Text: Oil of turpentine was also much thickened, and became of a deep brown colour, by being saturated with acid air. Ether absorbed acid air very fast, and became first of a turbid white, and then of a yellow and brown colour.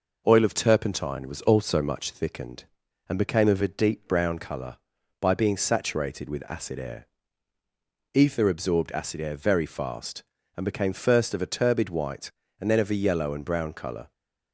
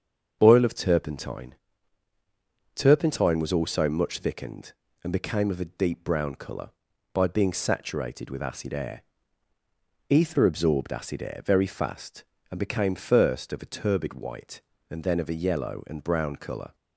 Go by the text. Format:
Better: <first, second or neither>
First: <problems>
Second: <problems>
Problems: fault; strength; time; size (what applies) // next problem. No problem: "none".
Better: first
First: none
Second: starts louder than the rest; strong; until 1.4 s; 7 dB // says "turpentine" twice; at 2.7 s